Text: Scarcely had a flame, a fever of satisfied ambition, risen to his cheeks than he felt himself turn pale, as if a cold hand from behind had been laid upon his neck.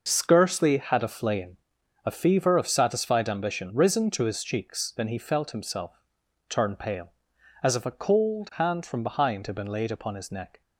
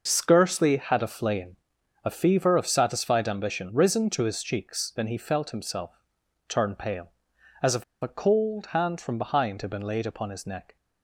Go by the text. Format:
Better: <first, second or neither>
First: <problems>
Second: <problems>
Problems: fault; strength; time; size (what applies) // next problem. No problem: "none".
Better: first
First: pauses between "himself" and "turn"; noticeable; at 5.9 s; 0.48 s long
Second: pauses between "himself" and "turn"; noticeable; at 5.9 s; 0.48 s long // pauses between "if" and "a"; slight; at 7.8 s; 0.17 s long